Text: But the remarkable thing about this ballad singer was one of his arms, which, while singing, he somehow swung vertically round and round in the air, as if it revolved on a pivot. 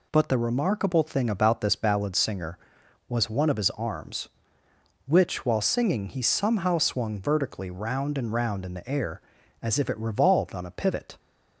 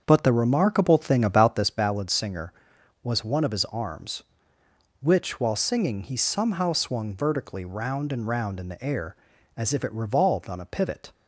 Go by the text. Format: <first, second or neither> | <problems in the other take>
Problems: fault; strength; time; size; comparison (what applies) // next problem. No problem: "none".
first | starts louder than the rest; until 1.7 s; 7 dB